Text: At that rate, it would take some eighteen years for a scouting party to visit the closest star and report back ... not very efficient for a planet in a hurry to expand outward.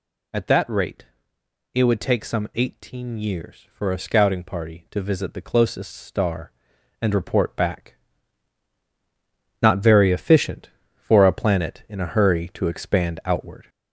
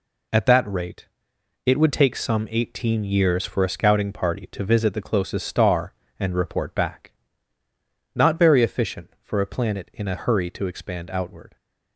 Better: second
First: gets louder; slight; throughout; 3 dB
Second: none

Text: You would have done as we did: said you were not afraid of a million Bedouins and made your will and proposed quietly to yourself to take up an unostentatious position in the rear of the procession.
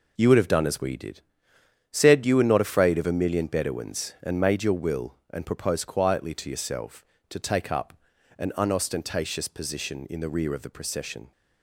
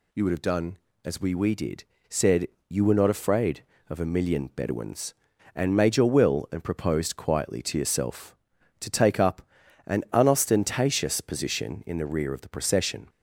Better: first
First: pauses between "up" and "an"; noticeable; at 7.9 s; 0.46 s long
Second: says "we" twice; at 1.3 s // pauses between "said" and "you"; slight; at 2.4 s; 0.22 s long // pauses between "up" and "an"; at 9.4 s; 0.44 s long

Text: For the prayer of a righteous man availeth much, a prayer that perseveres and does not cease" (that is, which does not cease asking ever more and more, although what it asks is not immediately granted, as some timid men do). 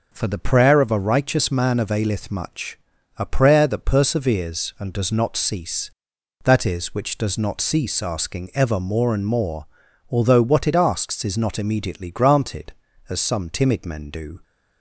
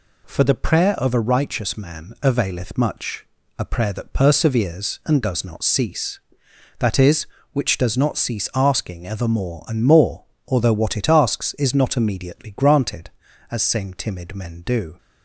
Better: first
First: none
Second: says "same" for "some"; at 13.6 s

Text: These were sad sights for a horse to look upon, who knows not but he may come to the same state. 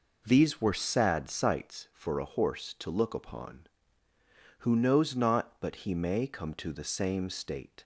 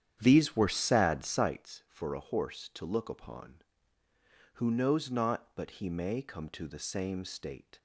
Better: first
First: none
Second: starts louder than the rest; strong; until 1.6 s; 9.5 dB

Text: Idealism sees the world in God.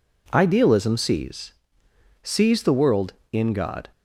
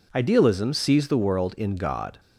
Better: second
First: says "sees" twice; at 2.2 s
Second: none

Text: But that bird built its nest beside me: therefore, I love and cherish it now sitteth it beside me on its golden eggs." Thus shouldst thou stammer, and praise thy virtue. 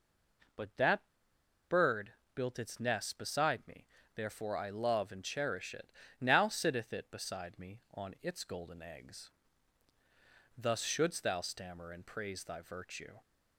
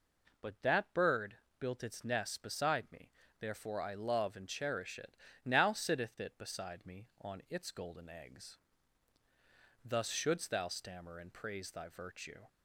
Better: second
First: pauses between "that" and "bird"; noticeable; at 1.0 s; 0.63 s long // pauses between "bird" and "built"; slight; at 2.1 s; 0.24 s long // pauses between "it" and "now"; slight; at 5.9 s; 0.28 s long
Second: pauses between "bird" and "built"; slight; at 1.3 s; 0.24 s long // pauses between "it" and "now"; slight; at 5.1 s; 0.28 s long

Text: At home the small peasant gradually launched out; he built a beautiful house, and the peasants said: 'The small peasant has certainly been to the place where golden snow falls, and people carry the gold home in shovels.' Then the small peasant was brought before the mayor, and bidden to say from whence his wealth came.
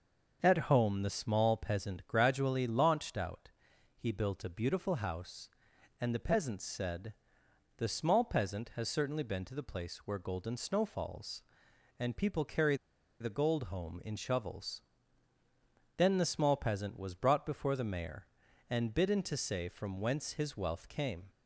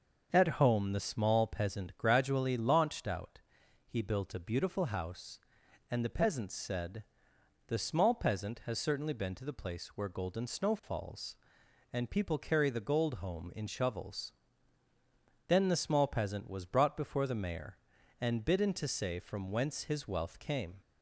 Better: second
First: starts louder than the rest; until 1.4 s; 6 dB // pauses between "carry" and "the"; at 12.7 s; 0.45 s long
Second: starts louder than the rest; until 1.3 s; 6 dB

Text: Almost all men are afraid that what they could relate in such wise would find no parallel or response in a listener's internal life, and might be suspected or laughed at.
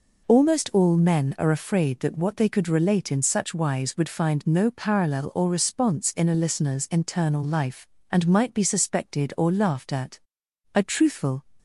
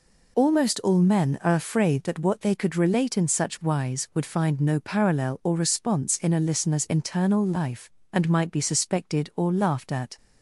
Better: second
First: goes on to say "A truthful"; noticeable; from 10.7 s on; 0.68 s long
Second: none

